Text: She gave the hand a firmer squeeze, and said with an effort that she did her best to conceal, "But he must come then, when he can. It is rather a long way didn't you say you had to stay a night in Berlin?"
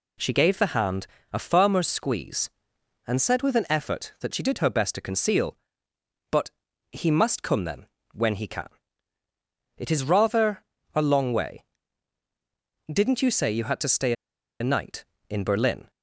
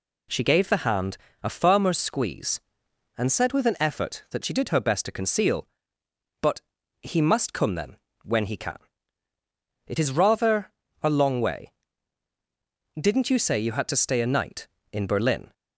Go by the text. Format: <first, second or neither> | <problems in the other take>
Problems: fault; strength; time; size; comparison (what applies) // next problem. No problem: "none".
second | pauses between "hand" and "a"; slight; at 1.0 s; 0.26 s long; slight in the second // pauses between "But" and "he"; at 6.5 s; 0.40 s long; also in the second // pauses between "rather" and "a"; slight; at 10.6 s; 0.28 s long; slight in the second // pauses between "way" and "didn't"; strong; at 11.6 s; 1.2 s long; strong in the second // pauses between "stay" and "a"; noticeable; at 14.1 s; 0.47 s long